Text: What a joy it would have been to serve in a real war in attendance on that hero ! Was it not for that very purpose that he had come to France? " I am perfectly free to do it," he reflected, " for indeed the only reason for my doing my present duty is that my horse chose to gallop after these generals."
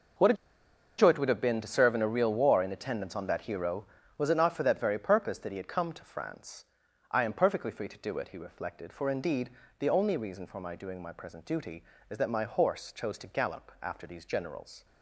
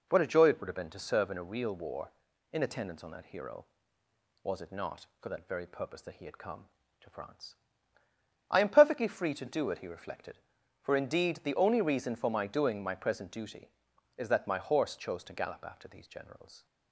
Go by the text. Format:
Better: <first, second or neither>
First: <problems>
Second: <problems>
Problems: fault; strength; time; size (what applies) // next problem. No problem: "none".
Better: second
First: pauses between "a" and "joy"; noticeable; at 0.3 s; 0.64 s long // pauses between "indeed" and "the"; slight; at 9.4 s; 0.30 s long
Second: none